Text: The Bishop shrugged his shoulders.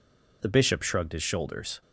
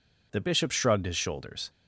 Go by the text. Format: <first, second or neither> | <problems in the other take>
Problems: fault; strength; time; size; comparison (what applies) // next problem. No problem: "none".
neither | none